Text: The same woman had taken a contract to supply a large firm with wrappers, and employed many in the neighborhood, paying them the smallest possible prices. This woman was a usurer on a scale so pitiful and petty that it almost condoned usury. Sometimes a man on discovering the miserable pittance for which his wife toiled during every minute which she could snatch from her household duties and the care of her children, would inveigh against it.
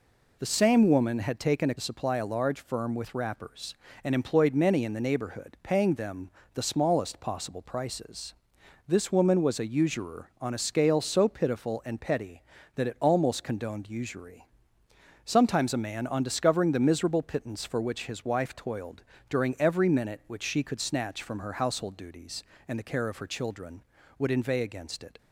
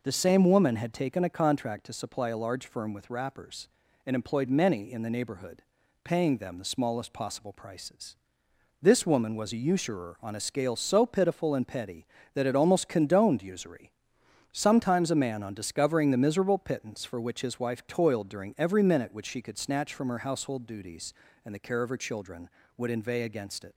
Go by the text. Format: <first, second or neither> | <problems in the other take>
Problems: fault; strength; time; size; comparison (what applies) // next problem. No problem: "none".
second | skips "contract to"; at 1.7 s // pauses between "them" and "the"; slight; at 6.2 s; 0.24 s long // pauses between "toiled" and "during"; slight; at 19.0 s; 0.28 s long